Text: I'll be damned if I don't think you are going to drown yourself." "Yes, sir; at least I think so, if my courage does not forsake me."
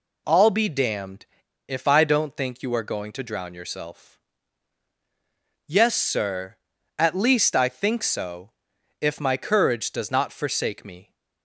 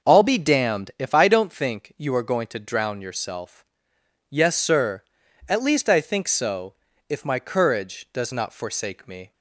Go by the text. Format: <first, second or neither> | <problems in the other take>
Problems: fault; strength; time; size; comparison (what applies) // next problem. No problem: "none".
second | pauses between "damned" and "if"; at 1.2 s; 0.40 s long